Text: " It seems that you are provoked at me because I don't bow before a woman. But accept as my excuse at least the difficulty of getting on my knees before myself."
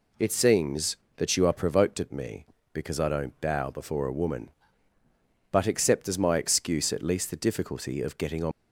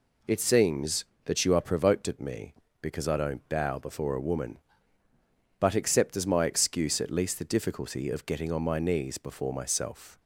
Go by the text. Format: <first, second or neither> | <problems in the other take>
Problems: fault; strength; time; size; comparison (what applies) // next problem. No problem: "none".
second | stops before "my knees before myself"; at 8.5 s